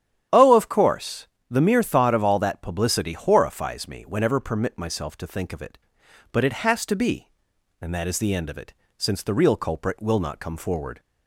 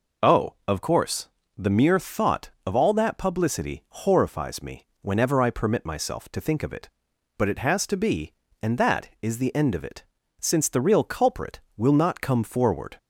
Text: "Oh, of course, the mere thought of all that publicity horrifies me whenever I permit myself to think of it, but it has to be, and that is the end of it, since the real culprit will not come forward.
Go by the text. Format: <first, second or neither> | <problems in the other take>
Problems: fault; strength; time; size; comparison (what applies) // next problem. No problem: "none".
second | starts louder than the rest; strong; until 1.5 s; 10 dB // skips "I"; at 4.3 s